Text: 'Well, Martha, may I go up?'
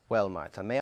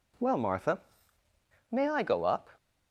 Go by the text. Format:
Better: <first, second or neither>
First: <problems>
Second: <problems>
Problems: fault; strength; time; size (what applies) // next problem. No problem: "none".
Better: second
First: stops before "I go up"; at 0.7 s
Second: none